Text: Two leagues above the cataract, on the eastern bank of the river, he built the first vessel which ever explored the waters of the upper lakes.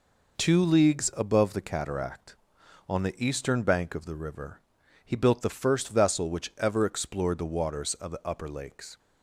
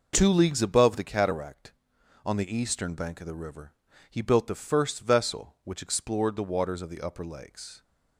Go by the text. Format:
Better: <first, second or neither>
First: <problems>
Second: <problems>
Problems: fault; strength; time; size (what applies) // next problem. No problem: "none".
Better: first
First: none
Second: skips "ever"; at 5.8 s